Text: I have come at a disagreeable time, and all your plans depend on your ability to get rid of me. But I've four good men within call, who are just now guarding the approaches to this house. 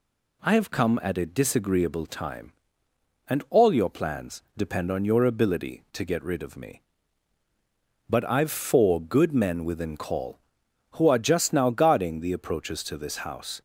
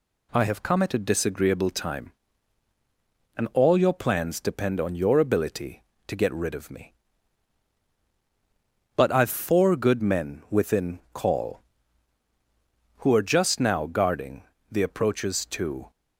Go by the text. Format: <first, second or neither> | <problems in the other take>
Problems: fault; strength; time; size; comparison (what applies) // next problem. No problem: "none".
first | pauses between "guarding" and "the"; slight; at 14.4 s; 0.28 s long // stops before "this house"; at 15.9 s